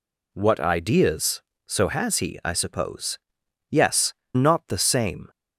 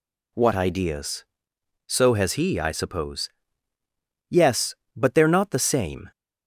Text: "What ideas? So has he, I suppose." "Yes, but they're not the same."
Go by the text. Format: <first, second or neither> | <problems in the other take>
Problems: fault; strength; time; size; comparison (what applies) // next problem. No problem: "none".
second | skips "but they're"; at 4.2 s